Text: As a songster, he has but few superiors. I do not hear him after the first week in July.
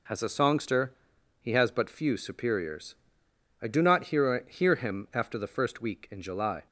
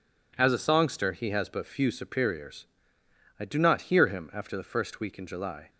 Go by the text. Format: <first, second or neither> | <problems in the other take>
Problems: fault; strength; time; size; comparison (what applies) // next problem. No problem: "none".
second | says "hear" twice; at 4.4 s